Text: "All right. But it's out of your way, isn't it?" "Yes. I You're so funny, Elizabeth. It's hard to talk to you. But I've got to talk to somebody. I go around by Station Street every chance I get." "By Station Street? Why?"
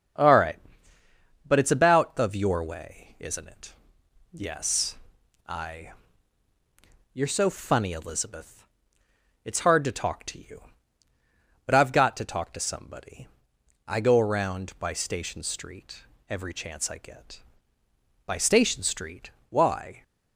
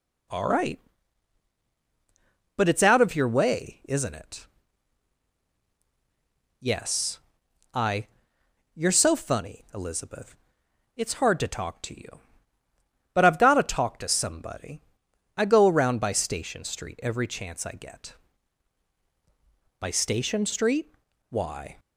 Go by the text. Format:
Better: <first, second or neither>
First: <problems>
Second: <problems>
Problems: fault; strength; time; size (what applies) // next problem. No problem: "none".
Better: second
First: starts louder than the rest; strong; until 2.0 s; 7.5 dB // says "about" for "out"; at 1.7 s // pauses between "I" and "You're"; at 5.9 s; 1.2 s long // pauses between "Street" and "every"; slight; at 16.0 s; 0.24 s long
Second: pauses between "I" and "You're"; noticeable; at 8.0 s; 0.66 s long